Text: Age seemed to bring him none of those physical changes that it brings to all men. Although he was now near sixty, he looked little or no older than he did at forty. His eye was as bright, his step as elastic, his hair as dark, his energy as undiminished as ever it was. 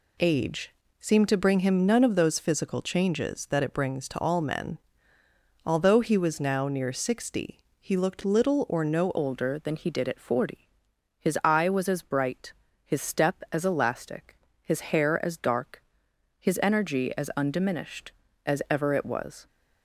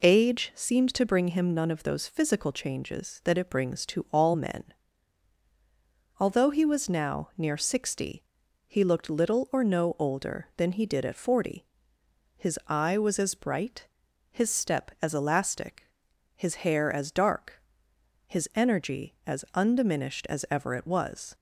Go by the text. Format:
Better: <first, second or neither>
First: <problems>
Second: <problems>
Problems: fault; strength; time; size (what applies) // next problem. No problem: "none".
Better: second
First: pauses between "Age" and "seemed"; slight; at 0.7 s; 0.28 s long // changes voice at "older"; from 9.1 s on; 10.3 s long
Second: none